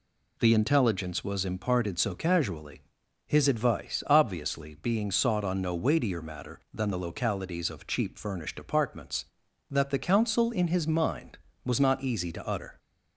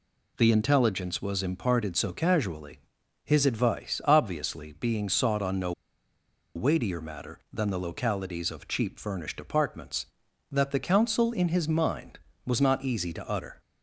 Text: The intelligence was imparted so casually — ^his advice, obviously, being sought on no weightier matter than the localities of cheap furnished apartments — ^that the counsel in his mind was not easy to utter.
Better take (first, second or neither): first